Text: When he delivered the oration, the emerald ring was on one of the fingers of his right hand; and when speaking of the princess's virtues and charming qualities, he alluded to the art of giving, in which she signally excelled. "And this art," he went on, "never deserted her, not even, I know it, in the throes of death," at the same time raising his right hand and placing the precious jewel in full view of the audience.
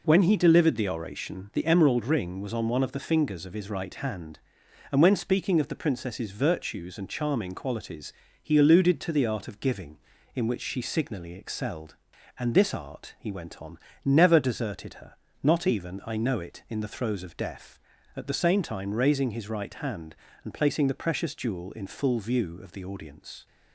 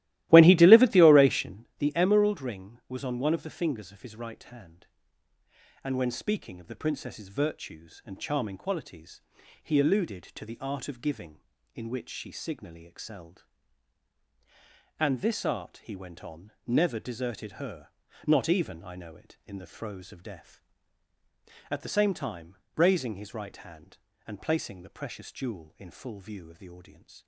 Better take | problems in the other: first | starts louder than the rest; strong; until 1.7 s; 16 dB // pauses between "time" and "raising"; slight; at 22.5 s; 0.20 s long

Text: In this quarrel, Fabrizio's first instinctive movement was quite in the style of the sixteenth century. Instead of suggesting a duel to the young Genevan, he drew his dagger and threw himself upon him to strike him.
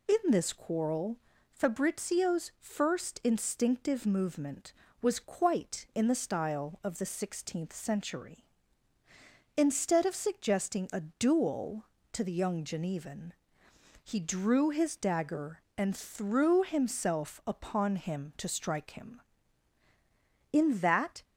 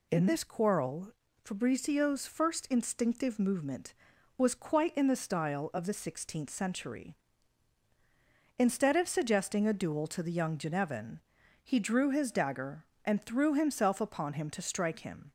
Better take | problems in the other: second | goes on to say "In that"; noticeable; from 20.5 s on; 0.72 s long

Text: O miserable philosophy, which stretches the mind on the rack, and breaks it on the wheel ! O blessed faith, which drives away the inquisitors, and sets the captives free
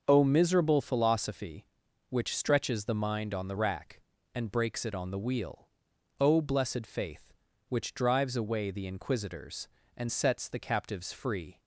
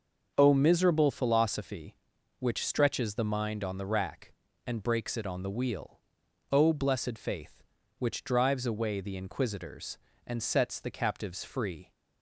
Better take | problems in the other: neither | starts louder than the rest; the same in both

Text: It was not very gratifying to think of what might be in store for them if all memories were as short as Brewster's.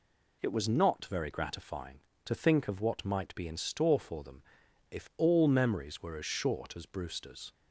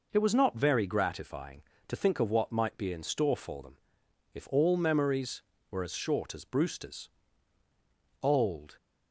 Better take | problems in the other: first | pauses between "them" and "if"; noticeable; at 3.7 s; 0.58 s long; noticeable in the first // goes on to say "Old"; from 8.2 s on; 0.54 s long

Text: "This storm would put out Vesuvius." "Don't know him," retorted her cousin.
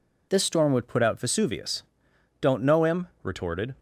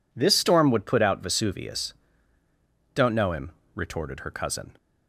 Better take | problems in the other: second | stops before "her cousin"; at 3.7 s

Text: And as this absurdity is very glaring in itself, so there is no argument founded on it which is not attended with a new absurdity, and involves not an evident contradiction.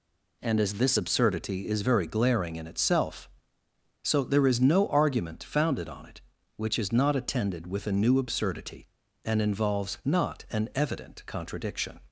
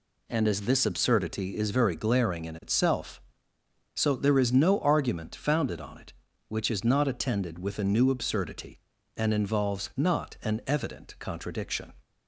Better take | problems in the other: neither | none

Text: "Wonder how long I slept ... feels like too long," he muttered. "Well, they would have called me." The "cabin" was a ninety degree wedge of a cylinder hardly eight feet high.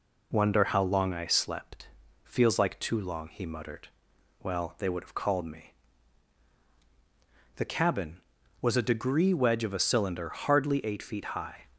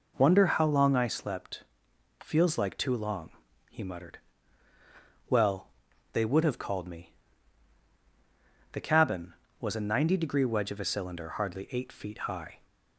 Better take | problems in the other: second | skips "ninety"; at 8.8 s

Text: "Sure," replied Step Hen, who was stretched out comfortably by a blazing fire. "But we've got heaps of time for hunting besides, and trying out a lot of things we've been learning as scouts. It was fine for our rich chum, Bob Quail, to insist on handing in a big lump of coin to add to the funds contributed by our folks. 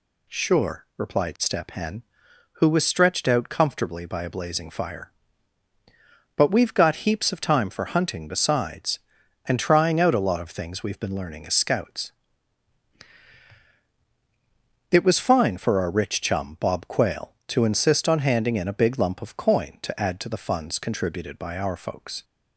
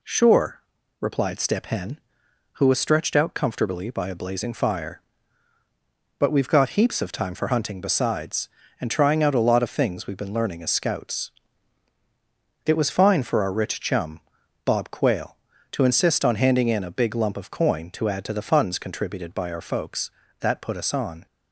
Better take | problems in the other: first | goes on to say "That put us on"; noticeable; from 20.3 s on; 0.86 s long

